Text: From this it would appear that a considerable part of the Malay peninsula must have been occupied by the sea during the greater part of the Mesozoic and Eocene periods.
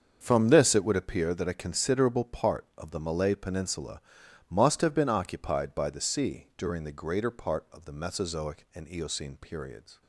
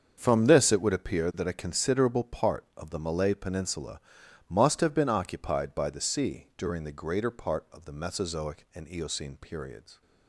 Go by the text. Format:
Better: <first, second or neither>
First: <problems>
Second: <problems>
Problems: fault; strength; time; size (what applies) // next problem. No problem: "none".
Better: neither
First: starts louder than the rest; until 1.2 s; 7 dB // pauses between "peninsula" and "must"; noticeable; at 3.9 s; 0.50 s long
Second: starts louder than the rest; until 1.1 s; 7 dB // pauses between "peninsula" and "must"; noticeable; at 3.9 s; 0.50 s long